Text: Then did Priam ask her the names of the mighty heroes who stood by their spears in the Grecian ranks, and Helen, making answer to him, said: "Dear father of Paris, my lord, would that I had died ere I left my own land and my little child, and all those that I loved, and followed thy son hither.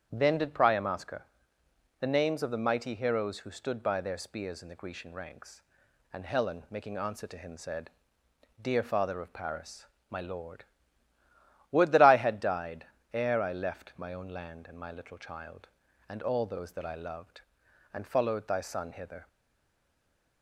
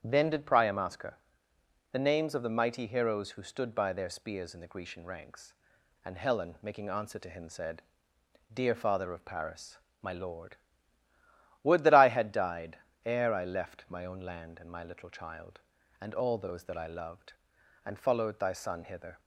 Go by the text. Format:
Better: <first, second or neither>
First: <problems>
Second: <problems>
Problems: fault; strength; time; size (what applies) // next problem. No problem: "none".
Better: second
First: starts louder than the rest; strong; until 1.1 s; 8.5 dB // pauses between "her" and "the"; noticeable; at 1.2 s; 0.74 s long // pauses between "died" and "ere"; slight; at 12.8 s; 0.26 s long // stays silent after the last word; noticeable; from 19.2 s on; 1.2 s long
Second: starts louder than the rest; strong; until 1.0 s; 8.5 dB // pauses between "her" and "the"; noticeable; at 1.1 s; 0.74 s long // pauses between "died" and "ere"; slight; at 12.7 s; 0.26 s long